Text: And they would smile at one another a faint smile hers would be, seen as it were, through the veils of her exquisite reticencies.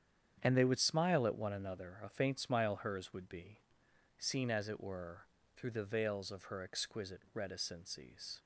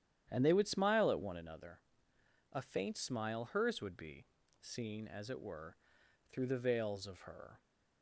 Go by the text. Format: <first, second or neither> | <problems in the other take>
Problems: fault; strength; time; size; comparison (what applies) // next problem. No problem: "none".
first | starts louder than the rest; strong; until 1.3 s; 10 dB; strong in the first // pauses between "another" and "a"; noticeable; at 1.8 s; 0.72 s long // stops before "exquisite reticencies"; at 7.6 s